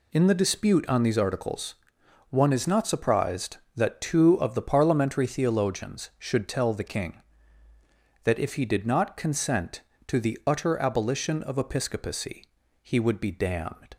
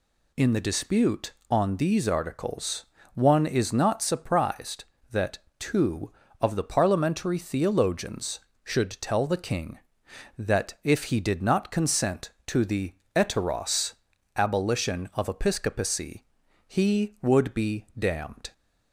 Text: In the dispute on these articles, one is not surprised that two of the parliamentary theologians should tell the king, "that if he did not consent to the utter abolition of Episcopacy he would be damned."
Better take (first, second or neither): first